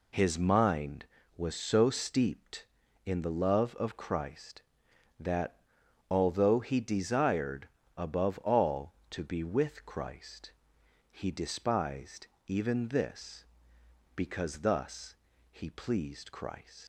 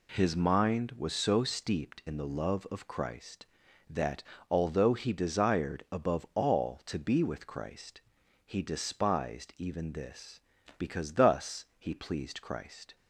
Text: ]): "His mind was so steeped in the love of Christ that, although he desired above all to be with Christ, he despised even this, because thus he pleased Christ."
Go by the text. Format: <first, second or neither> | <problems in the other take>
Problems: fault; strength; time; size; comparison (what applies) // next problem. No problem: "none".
second | pauses between "desired" and "above"; slight; at 7.6 s; 0.30 s long // pauses between "despised" and "even"; slight; at 12.2 s; 0.20 s long // pauses between "thus" and "he"; slight; at 15.1 s; 0.36 s long // leaves "Christ" unfinished; at 16.8 s; 90 ms